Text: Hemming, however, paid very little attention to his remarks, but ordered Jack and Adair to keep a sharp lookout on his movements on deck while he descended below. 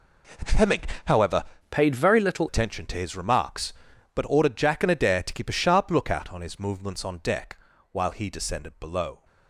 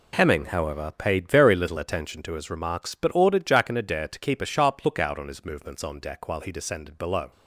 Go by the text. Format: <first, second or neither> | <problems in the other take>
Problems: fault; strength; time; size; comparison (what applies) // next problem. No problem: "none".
second | changes voice from "paid" to "little"; from 1.6 to 2.4 s; 0.8 s long // pauses between "deck" and "while"; slight; at 7.5 s; 0.34 s long